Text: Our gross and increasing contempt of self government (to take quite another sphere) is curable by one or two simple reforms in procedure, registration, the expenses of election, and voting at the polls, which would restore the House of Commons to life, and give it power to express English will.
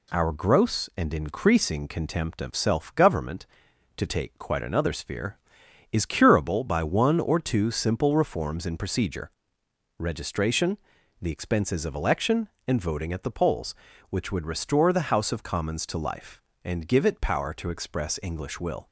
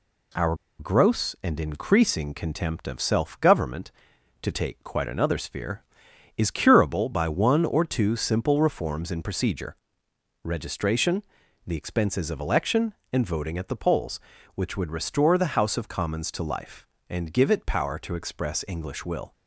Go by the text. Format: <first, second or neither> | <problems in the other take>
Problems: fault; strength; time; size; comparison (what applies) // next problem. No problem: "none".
first | pauses between "Our" and "gross"; slight; at 0.5 s; 0.23 s long